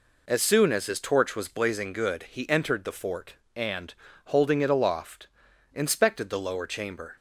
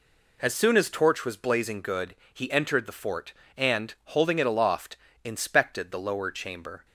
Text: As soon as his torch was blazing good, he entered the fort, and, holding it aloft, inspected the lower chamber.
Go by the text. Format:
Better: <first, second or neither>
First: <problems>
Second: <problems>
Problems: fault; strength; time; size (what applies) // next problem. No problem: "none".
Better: first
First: none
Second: skips "his"; at 0.8 s